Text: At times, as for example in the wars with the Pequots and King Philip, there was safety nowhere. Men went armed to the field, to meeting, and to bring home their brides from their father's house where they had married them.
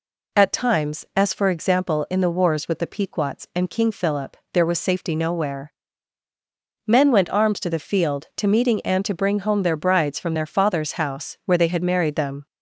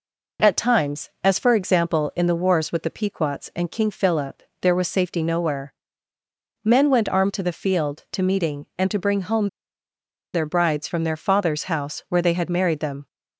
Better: first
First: none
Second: pauses between "home" and "their"; noticeable; at 9.4 s; 0.85 s long

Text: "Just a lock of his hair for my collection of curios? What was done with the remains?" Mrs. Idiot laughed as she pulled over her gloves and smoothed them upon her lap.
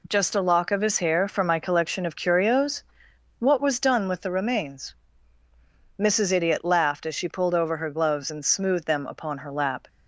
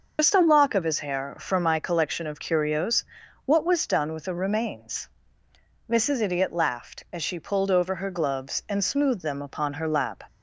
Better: first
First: none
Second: loses the start of "Just"; at 0.1 s; 95 ms

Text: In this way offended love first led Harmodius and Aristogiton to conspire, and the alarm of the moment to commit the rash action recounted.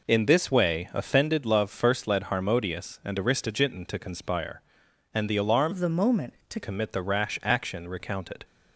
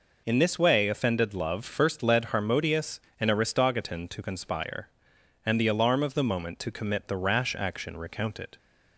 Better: second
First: changes voice from "of" to "to"; from 5.7 to 6.5 s; 0.8 s long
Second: none

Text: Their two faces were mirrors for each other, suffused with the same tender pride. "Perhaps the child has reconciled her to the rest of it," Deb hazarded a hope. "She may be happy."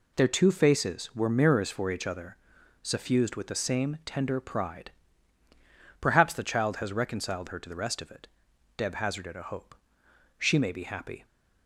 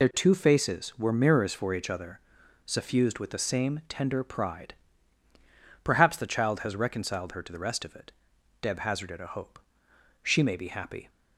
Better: first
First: none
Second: loses the start of "Their"; at 0.0 s; 45 ms

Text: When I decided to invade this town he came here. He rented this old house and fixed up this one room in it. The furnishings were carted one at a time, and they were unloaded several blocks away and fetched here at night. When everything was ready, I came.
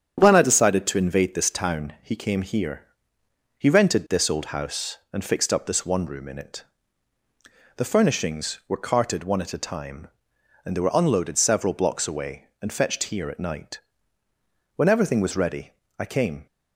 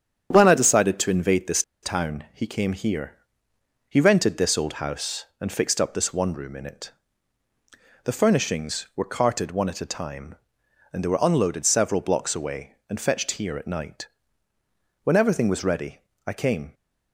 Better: first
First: starts louder than the rest; strong; until 1.2 s; 8 dB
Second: starts louder than the rest; strong; until 1.3 s; 8 dB // pauses between "this" and "town"; slight; at 1.6 s; 0.21 s long

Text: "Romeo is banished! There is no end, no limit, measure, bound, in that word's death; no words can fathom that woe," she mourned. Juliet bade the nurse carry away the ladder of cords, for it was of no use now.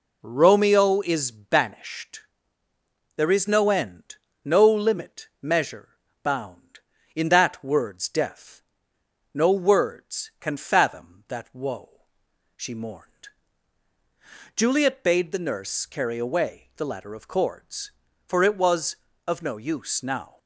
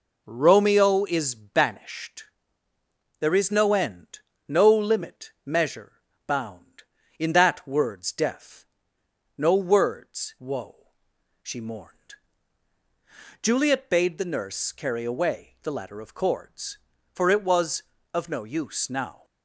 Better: first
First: none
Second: skips "can fathom that"; at 10.3 s

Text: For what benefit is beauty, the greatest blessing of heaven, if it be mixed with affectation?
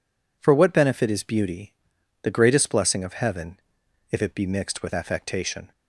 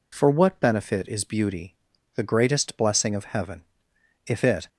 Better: first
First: none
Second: stops before "be mixed with affectation"; at 4.6 s

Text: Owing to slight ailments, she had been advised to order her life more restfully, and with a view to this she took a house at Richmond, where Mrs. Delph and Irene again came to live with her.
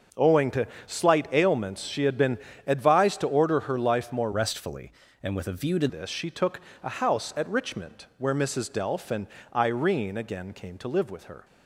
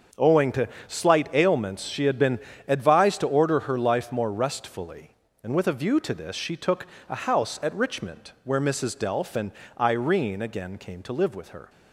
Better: second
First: starts louder than the rest; noticeable; until 1.3 s; 6 dB // pauses between "to" and "slight"; slight; at 0.6 s; 0.18 s long // pauses between "been" and "advised"; slight; at 2.3 s; 0.28 s long // changes voice from "restfully" to "to"; from 4.3 to 5.8 s; 1.5 s long // pauses between "took" and "a"; slight; at 6.6 s; 0.22 s long // pauses between "and" and "Irene"; slight; at 9.2 s; 0.28 s long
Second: starts louder than the rest; until 1.4 s; 7 dB // pauses between "to" and "slight"; slight; at 0.6 s; 0.18 s long // pauses between "been" and "advised"; slight; at 2.3 s; 0.28 s long // pauses between "took" and "a"; slight; at 6.8 s; 0.22 s long // pauses between "and" and "Irene"; slight; at 9.5 s; 0.28 s long

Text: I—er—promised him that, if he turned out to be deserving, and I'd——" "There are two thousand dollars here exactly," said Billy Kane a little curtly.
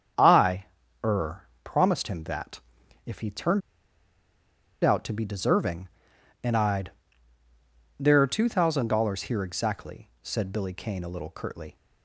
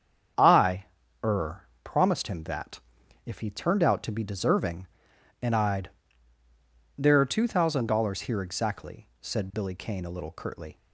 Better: second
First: starts louder than the rest; strong; until 1.7 s; 7.5 dB // pauses between "turned" and "out"; at 3.6 s; 1.2 s long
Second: starts louder than the rest; strong; until 1.9 s; 7.5 dB

